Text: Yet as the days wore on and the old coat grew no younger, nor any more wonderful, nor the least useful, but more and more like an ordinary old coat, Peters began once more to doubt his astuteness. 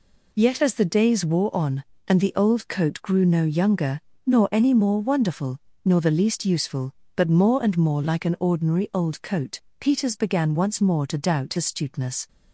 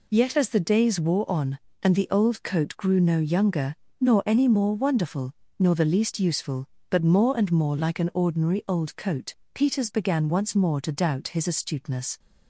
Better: second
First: skips "his"; at 11.5 s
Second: none

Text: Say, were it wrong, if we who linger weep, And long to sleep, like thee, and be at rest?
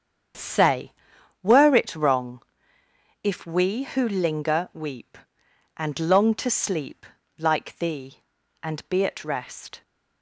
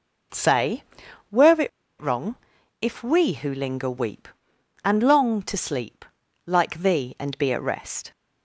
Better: first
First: starts louder than the rest; strong; until 1.9 s; 7.5 dB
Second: starts louder than the rest; until 2.1 s; 6.5 dB // pauses between "it" and "wrong"; slight; at 1.6 s; 0.31 s long

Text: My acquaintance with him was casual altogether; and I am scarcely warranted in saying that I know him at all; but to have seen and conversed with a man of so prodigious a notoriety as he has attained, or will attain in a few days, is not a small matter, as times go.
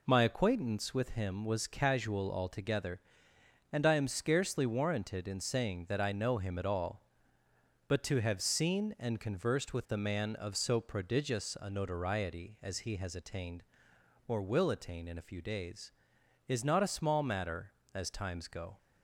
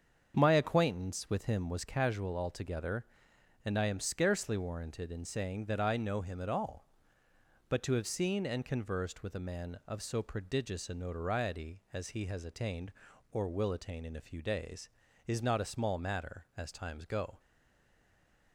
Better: first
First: none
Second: starts louder than the rest; strong; until 1.4 s; 7 dB // stays silent after the last word; noticeable; from 17.3 s on; 1.2 s long

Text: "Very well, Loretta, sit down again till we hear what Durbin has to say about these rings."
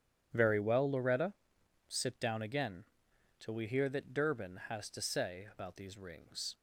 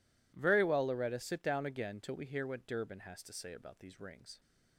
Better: second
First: pauses between "again" and "till"; noticeable; at 2.8 s; 0.54 s long // says "that" for "what"; at 3.8 s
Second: none

